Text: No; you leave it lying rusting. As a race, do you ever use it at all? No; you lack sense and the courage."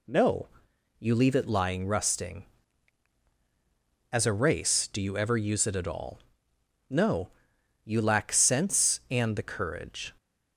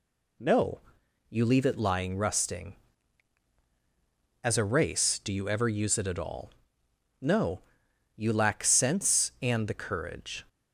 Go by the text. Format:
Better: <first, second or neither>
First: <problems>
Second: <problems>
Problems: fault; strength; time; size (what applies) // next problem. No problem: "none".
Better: neither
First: none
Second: none